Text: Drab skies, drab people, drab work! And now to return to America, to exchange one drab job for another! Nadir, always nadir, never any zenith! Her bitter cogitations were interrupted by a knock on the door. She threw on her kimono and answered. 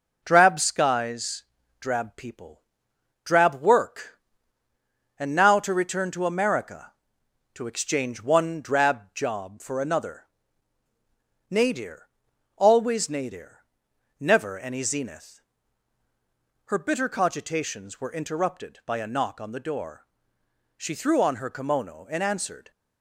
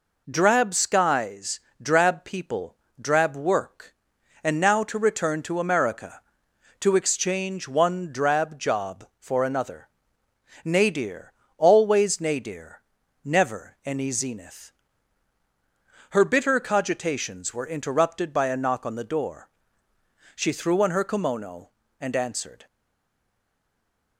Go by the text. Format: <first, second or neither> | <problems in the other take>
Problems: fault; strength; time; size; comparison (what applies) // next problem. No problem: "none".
first | stays silent after the last word; noticeable; from 22.6 s on; 1.5 s long